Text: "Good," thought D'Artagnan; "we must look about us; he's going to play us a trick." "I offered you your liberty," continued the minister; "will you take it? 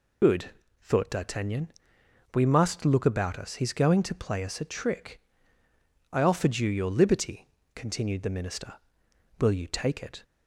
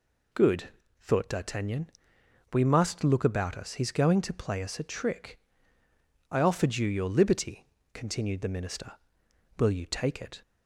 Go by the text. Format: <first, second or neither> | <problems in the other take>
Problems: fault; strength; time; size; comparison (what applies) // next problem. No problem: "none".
second | loses the start of "Good"; at 0.2 s; 70 ms